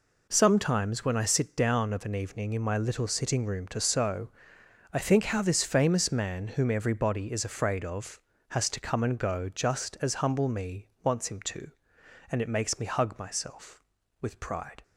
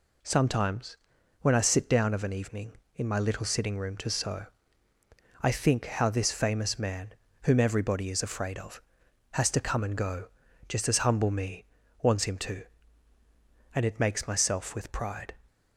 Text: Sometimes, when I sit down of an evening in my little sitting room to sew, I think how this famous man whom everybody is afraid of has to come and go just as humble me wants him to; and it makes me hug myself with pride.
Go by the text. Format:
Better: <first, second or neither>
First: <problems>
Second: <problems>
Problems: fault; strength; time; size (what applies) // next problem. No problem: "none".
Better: first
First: pauses between "me" and "wants"; slight; at 10.8 s; 0.16 s long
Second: pauses between "man" and "whom"; slight; at 7.1 s; 0.30 s long // pauses between "go" and "just"; at 10.2 s; 0.42 s long // pauses between "me" and "wants"; at 11.6 s; 0.38 s long // skips "me hug"; at 14.2 s